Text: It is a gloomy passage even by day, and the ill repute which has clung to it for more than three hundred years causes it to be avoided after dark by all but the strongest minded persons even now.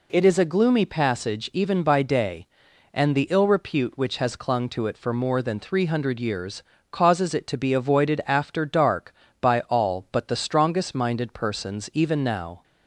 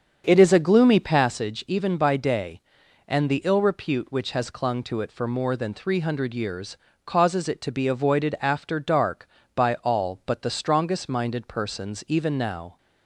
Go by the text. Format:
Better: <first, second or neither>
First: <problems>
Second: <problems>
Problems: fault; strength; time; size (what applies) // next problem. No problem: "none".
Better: first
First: pauses between "years" and "causes"; slight; at 6.6 s; 0.28 s long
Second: starts louder than the rest; strong; until 1.4 s; 7 dB // pauses between "years" and "causes"; slight; at 6.7 s; 0.28 s long